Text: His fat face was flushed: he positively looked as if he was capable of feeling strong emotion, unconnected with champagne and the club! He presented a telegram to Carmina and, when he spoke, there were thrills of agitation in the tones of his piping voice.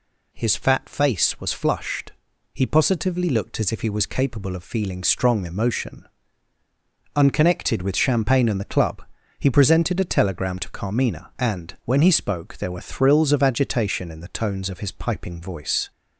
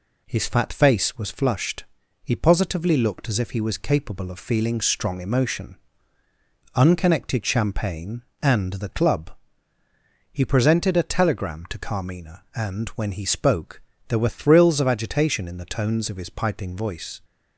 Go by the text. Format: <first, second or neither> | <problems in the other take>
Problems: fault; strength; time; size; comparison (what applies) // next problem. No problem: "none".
first | skips "with"; at 7.4 s